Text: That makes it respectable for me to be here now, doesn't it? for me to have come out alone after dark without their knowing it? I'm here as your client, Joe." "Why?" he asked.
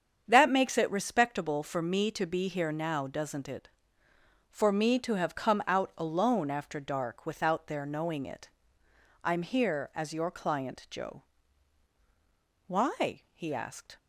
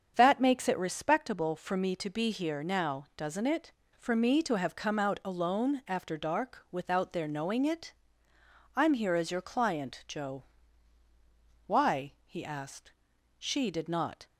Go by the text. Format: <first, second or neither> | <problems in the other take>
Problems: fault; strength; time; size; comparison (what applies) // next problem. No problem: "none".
first | starts louder than the rest; strong; until 1.1 s; 7.5 dB; strong in the first // goes on to say "She did not"; noticeable; from 13.3 s on; 0.88 s long